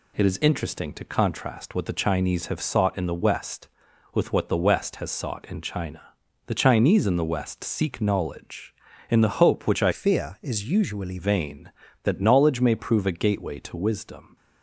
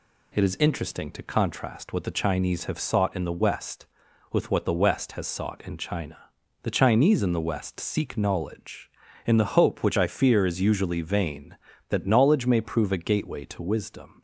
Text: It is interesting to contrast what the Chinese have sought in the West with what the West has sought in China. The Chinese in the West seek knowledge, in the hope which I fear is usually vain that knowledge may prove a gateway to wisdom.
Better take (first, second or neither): second